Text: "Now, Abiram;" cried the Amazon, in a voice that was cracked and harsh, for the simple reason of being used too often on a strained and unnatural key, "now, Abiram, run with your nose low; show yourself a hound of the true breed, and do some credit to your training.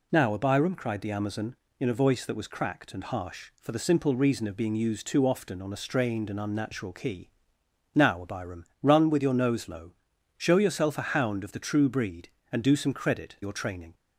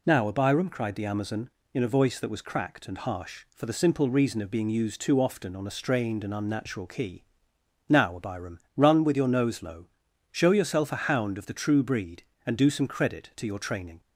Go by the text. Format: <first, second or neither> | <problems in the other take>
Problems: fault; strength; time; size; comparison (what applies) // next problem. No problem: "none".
second | skips "to"; at 13.3 s